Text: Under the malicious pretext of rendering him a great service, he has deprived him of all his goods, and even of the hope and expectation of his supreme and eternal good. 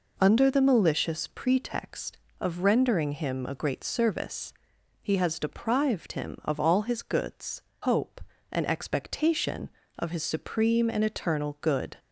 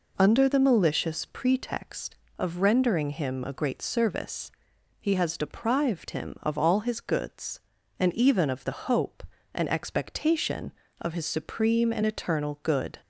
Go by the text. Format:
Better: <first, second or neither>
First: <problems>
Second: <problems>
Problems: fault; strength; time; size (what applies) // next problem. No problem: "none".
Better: second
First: skips "and even of the"; at 7.7 s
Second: none